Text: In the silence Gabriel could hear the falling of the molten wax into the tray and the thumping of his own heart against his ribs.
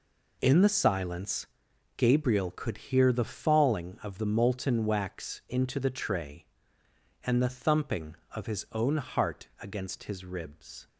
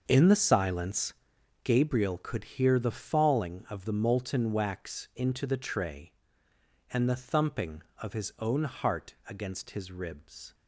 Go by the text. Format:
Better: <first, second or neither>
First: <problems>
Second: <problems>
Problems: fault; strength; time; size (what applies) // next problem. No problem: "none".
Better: first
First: pauses between "silence" and "Gabriel"; noticeable; at 1.4 s; 0.50 s long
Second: starts louder than the rest; until 1.7 s; 6.5 dB // pauses between "silence" and "Gabriel"; noticeable; at 1.1 s; 0.50 s long